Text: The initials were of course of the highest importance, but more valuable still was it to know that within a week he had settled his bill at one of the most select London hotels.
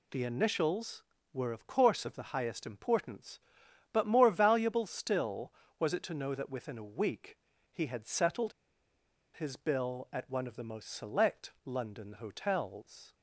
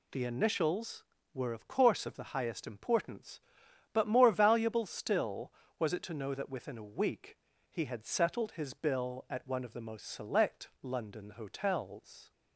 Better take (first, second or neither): second